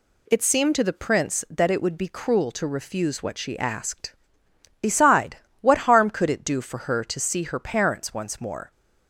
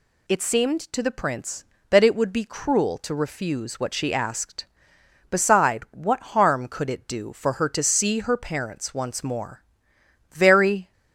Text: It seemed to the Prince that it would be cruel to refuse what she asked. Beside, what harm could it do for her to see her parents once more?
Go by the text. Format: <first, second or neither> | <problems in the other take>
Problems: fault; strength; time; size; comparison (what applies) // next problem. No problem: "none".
first | goes on to say "Very"; from 10.3 s on; 0.60 s long